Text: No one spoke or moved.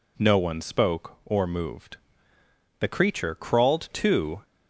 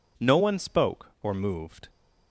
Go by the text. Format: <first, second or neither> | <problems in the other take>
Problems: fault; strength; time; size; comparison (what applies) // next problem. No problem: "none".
second | goes on to say "The creature crawled to"; from 2.7 s on; 1.6 s long